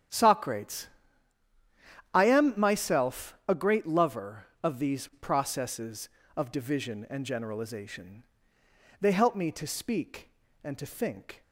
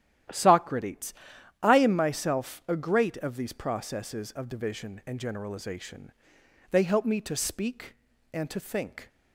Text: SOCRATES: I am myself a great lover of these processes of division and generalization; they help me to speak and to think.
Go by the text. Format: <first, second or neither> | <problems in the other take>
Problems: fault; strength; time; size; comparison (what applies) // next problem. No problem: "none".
first | starts louder than the rest; strong; until 1.7 s; 11.5 dB; strong in the first // skips "lover"; at 3.1 s